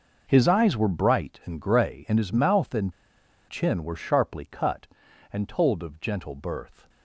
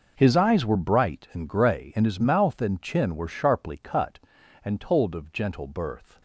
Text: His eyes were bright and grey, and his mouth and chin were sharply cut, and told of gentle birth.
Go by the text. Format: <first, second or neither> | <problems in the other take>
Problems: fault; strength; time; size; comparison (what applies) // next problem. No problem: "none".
second | pauses between "and" and "chin"; noticeable; at 2.9 s; 0.55 s long